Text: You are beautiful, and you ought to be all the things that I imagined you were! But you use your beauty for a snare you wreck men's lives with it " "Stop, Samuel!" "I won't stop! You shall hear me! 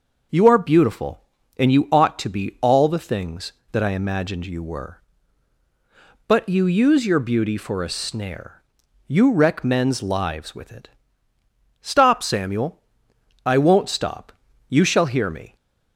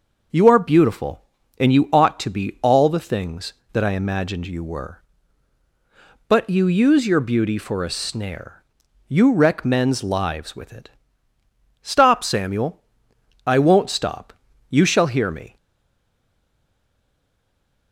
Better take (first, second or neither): first